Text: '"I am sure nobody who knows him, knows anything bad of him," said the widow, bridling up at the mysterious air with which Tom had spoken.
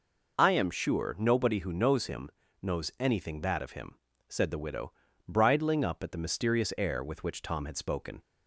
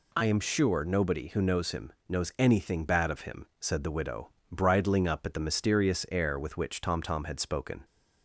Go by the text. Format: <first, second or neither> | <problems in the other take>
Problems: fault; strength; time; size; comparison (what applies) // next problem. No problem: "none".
first | says "Tom" twice; at 7.0 s